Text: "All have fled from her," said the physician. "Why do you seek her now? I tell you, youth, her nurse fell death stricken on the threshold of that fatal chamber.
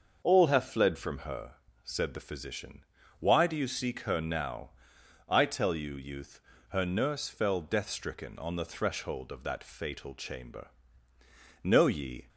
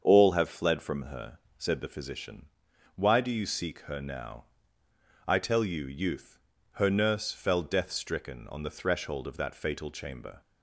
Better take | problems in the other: second | starts louder than the rest; noticeable; until 1.2 s; 6 dB; also in the second // goes on to say "Know ye"; noticeable; from 11.6 s on; 0.64 s long

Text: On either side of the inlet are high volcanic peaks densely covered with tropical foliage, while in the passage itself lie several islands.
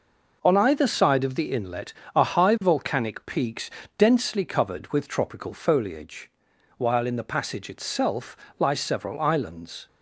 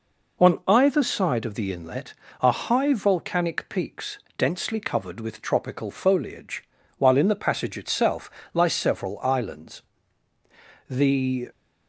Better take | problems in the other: first | pauses between "peaks" and "densely"; slight; at 4.1 s; 0.19 s long; slight in the first // pauses between "itself" and "lie"; slight; at 8.3 s; 0.24 s long; slight in the first // goes on to say "The"; noticeable; from 10.8 s on; 0.62 s long

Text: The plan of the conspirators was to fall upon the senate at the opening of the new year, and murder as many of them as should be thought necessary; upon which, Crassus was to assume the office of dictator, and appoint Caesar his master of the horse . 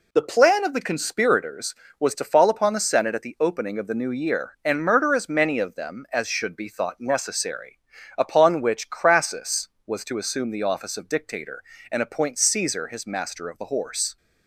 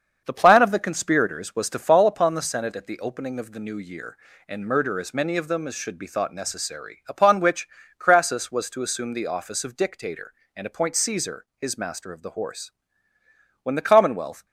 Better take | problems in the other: first | starts louder than the rest; until 1.2 s; 7 dB // goes on to say "When the commonwealth"; noticeable; from 13.6 s on; 0.82 s long

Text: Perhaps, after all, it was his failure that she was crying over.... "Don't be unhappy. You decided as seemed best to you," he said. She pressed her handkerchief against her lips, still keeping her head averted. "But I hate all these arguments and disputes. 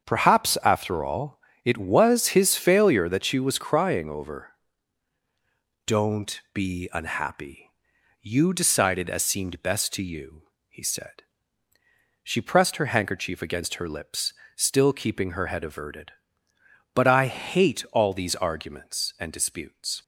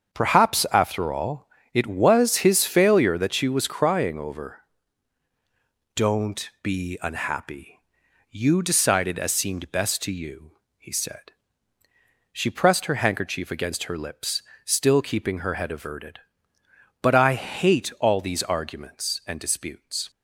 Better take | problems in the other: neither | starts louder than the rest; the same in both

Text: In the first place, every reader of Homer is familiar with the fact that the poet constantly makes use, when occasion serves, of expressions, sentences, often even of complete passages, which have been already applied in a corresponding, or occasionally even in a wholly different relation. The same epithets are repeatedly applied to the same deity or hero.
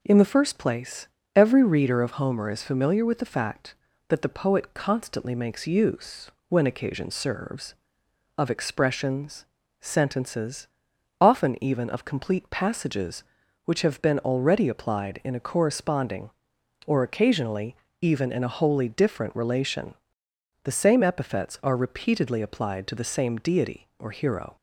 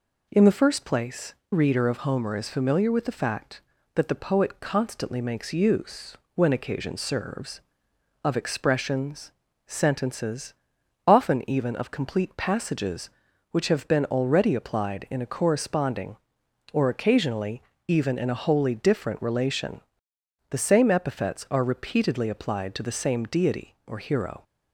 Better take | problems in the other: first | skips "every"; at 1.4 s // pauses between "occasionally" and "even"; slight; at 17.6 s; 0.26 s long; slight in the first

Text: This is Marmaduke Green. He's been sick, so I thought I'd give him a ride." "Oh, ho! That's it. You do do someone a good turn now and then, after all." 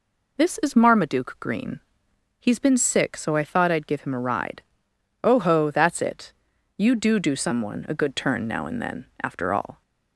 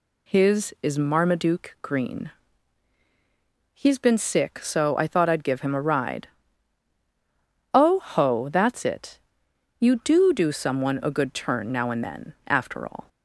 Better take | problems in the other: first | says "His" for "This"; at 0.2 s

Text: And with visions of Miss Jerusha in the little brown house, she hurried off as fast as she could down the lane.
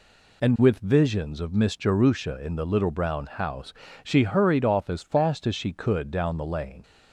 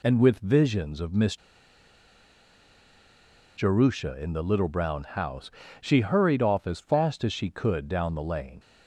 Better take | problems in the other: first | pauses between "Miss" and "Jerusha"; strong; at 1.3 s; 2.2 s long

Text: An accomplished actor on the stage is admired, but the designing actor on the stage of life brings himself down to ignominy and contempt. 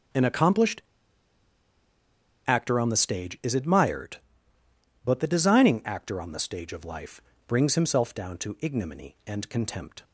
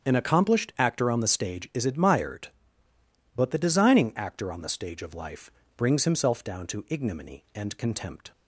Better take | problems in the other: second | starts louder than the rest; strong; until 2.8 s; 8.5 dB; strong in the second // pauses between "accomplished" and "actor"; strong; at 0.8 s; 1.6 s long // pauses between "life" and "brings"; slight; at 7.2 s; 0.26 s long; slight in the second

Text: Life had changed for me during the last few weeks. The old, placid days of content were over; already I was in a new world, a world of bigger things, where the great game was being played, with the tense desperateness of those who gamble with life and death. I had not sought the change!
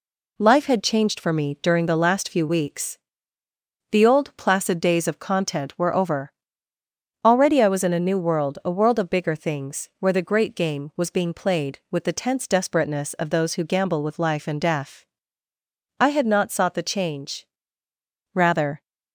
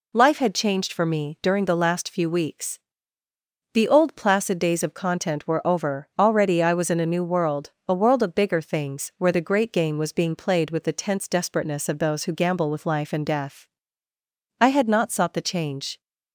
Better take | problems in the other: second | goes on to say "Rather"; slight; from 18.3 s on; 0.48 s long

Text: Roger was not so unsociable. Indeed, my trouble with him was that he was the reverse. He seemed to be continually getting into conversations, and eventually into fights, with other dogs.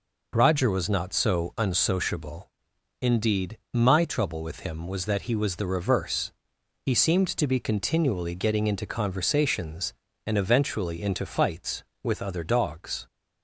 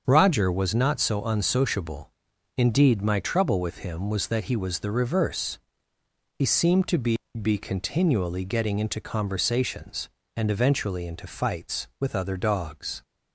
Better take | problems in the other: first | starts louder than the rest; until 1.0 s; 6.5 dB // says "be" twice; at 7.4 s

